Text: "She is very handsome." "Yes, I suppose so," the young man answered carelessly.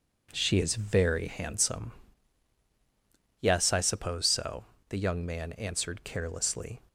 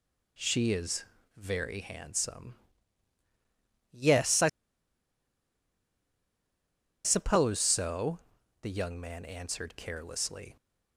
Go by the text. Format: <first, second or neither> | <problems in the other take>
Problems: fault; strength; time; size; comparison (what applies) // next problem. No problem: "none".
first | pauses between "is" and "very"; slight; at 1.0 s; 0.32 s long // pauses between "I" and "suppose"; strong; at 4.4 s; 2.5 s long